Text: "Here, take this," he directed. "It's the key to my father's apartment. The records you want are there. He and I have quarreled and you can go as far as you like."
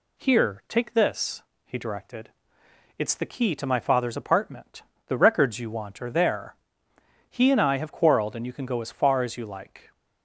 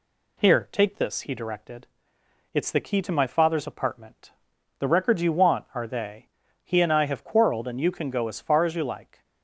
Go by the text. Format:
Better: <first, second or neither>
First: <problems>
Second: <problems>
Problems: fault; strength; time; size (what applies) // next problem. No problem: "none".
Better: first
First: none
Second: says "they" for "there"; at 5.8 s